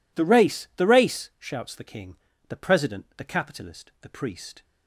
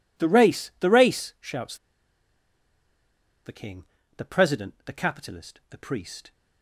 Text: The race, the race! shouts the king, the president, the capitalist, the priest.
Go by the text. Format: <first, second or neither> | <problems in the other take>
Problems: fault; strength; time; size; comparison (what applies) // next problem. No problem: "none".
first | pauses between "shouts" and "the"; strong; at 1.7 s; 1.6 s long